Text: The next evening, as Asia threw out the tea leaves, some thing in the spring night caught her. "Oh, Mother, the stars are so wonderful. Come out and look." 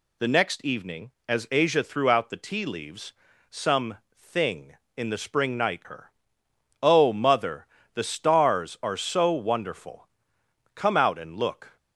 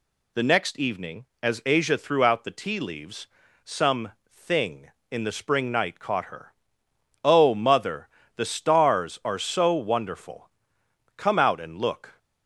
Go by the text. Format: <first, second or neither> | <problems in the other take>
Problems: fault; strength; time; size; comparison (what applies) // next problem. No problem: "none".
second | pauses between "some" and "thing"; slight; at 3.9 s; 0.18 s long; slight in the second // skips "caught"; at 5.8 s